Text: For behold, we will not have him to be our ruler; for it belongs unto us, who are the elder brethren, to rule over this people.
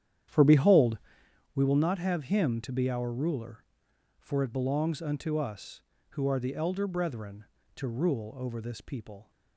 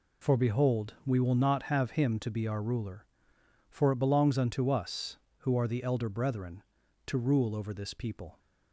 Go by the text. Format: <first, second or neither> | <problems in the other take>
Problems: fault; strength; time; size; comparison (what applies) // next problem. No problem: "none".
second | starts louder than the rest; strong; until 1.5 s; 10 dB